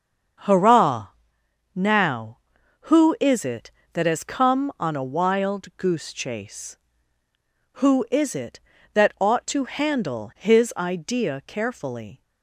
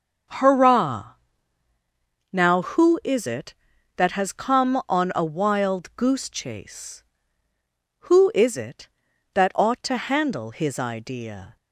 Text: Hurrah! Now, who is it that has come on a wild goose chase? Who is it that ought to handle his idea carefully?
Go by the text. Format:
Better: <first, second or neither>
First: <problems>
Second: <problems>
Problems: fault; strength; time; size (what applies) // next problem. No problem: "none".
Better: first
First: starts louder than the rest; until 2.1 s; 7 dB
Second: starts louder than the rest; until 2.4 s; 6.5 dB // stops before "carefully"; at 11.5 s